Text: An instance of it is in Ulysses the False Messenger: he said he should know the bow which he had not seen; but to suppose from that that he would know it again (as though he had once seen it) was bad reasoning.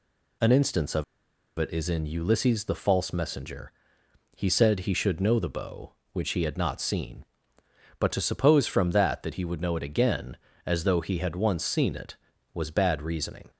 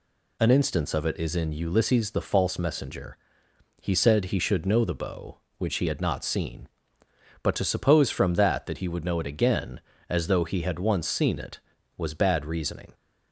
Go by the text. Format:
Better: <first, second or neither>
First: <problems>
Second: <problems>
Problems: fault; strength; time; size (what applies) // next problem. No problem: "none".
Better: second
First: pauses between "of" and "it"; noticeable; at 1.0 s; 0.53 s long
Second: none